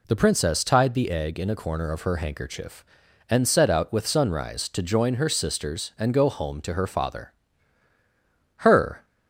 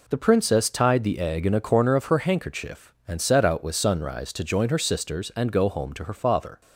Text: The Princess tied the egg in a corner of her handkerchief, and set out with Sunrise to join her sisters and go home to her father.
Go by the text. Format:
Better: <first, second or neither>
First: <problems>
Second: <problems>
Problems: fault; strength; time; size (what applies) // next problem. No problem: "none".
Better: second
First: goes on to say "Her"; slight; from 8.5 s on; 0.48 s long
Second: none